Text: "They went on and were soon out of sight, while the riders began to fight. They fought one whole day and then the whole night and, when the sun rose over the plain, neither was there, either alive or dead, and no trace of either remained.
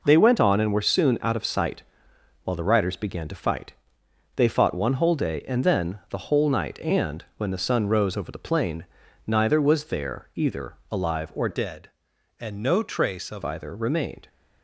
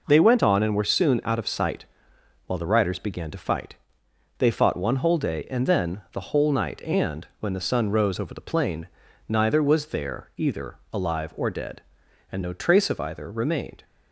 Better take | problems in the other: second | pauses between "either" and "alive"; slight; at 10.7 s; 0.16 s long; slight in the second // changes voice from "dead" to "of"; from 11.5 to 13.4 s; 1.9 s long

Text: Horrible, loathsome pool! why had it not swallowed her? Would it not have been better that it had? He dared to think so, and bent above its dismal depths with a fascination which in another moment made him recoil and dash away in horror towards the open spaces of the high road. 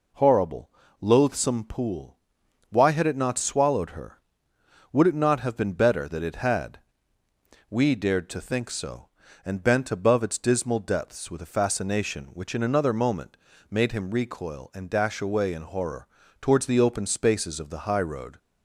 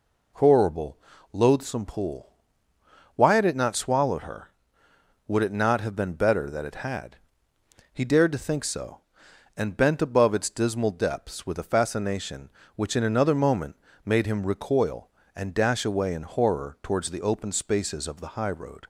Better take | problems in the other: second | says "We" for "He"; at 7.6 s // pauses between "moment" and "made"; slight; at 13.3 s; 0.34 s long; slight in the second // pauses between "horror" and "towards"; slight; at 16.0 s; 0.32 s long

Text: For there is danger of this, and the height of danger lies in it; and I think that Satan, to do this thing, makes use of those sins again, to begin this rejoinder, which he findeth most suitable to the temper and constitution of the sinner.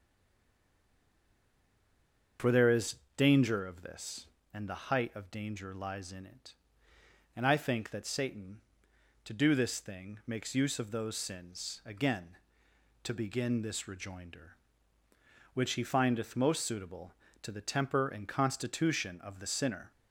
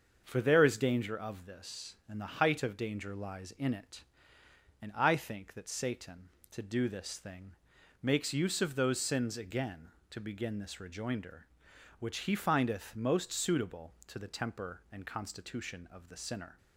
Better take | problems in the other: second | stays silent before the first word; until 2.3 s; 2.3 s long // starts louder than the rest; until 3.6 s; 7 dB; also in the second // pauses between "is" and "danger"; slight; at 2.9 s; 0.22 s long

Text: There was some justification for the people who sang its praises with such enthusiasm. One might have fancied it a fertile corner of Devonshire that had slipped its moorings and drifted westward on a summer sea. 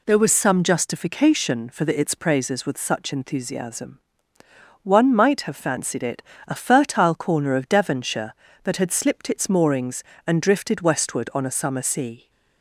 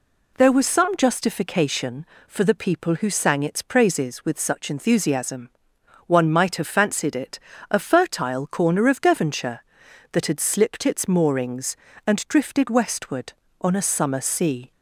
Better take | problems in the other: second | skips "people who sang"; at 1.9 s // pauses between "it" and "a"; slight; at 6.2 s; 0.24 s long; slight in the second

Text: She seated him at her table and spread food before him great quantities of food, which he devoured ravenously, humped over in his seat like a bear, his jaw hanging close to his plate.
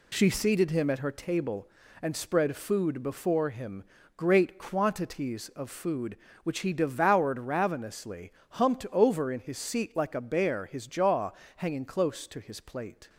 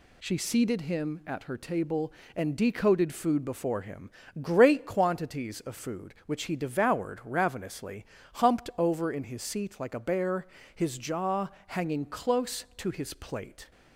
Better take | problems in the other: first | says "decoded" for "spread"; at 2.5 s // pauses between "him" and "great"; slight; at 4.1 s; 0.30 s long; slight in the first // pauses between "jaw" and "hanging"; slight; at 11.4 s; 0.20 s long; slight in the first

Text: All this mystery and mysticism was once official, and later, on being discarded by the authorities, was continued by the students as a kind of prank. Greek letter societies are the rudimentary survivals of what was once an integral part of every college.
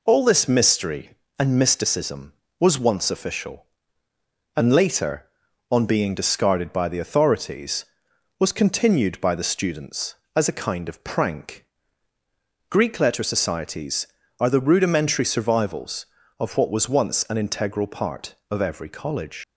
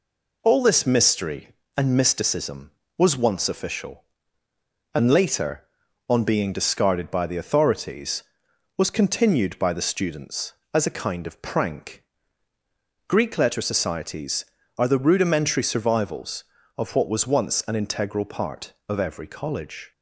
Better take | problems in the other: second | leaves "college" unfinished; at 19.4 s; 100 ms

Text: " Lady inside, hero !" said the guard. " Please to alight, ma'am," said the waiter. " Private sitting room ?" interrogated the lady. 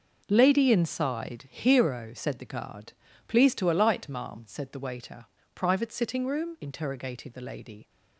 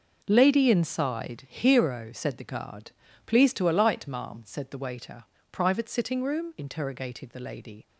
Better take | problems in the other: neither | none

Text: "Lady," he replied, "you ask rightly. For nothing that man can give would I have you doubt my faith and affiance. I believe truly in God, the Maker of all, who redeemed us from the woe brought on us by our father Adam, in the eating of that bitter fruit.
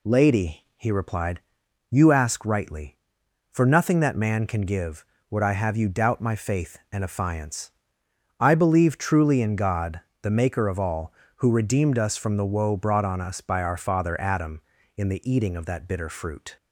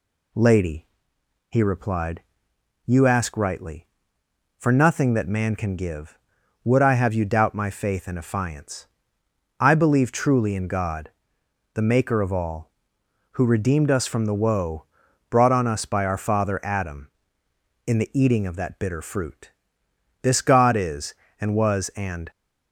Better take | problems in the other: first | pauses between "woe" and "brought"; noticeable; at 14.8 s; 0.46 s long // goes on to say "This God is and was and"; strong; from 20.2 s on; 2.0 s long

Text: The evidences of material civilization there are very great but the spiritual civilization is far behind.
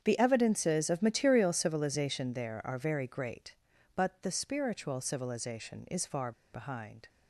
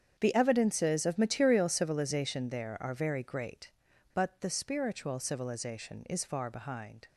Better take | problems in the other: second | starts louder than the rest; strong; until 1.0 s; 8 dB; strong in the second // pauses between "far" and "behind"; slight; at 6.3 s; 0.22 s long

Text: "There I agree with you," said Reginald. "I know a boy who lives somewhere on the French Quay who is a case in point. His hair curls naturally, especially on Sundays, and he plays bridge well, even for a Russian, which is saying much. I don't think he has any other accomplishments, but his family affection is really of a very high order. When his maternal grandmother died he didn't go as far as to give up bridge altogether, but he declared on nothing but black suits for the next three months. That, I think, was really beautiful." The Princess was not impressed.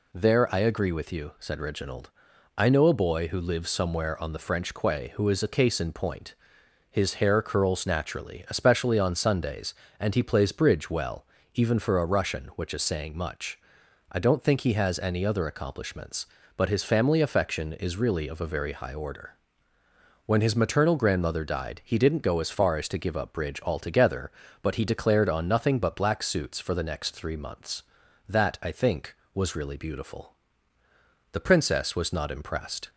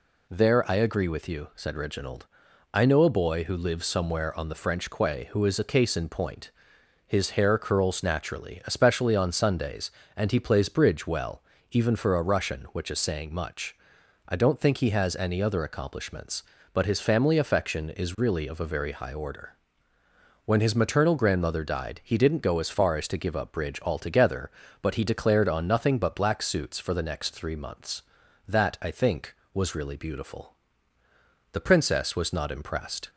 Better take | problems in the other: neither | none

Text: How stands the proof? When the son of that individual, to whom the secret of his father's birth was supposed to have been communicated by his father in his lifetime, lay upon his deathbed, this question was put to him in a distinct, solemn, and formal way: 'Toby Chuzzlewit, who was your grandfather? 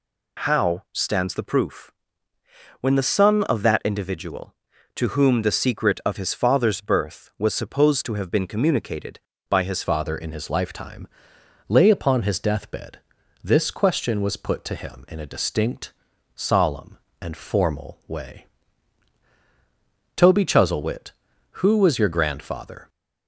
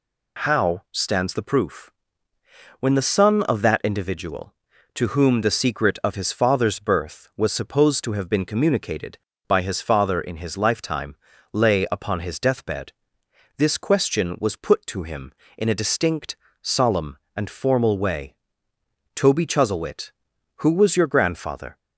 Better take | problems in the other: second | changes voice at "father"; from 9.8 s on; 13.0 s long

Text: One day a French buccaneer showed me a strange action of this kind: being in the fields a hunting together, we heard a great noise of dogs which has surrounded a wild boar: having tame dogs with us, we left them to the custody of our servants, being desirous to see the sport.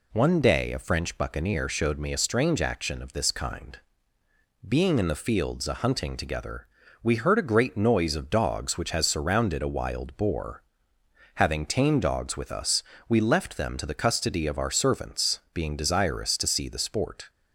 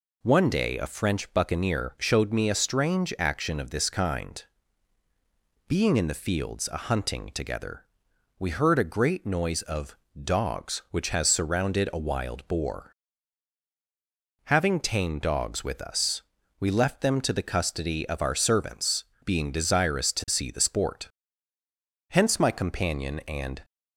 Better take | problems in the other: first | pauses between "of" and "dogs"; slight; at 9.9 s; 0.26 s long // goes on to say "Hence my companion and"; from 22.0 s on; 1.5 s long

